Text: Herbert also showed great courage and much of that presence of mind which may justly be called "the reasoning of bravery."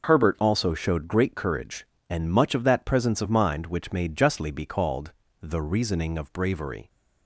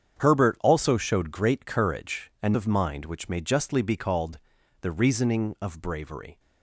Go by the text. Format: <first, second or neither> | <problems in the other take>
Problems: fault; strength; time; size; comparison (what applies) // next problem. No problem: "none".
first | starts louder than the rest; strong; until 1.2 s; 8 dB // skips "much of that presence"; at 2.5 s // pauses between "called" and "the"; at 4.3 s; 0.42 s long; slight in the first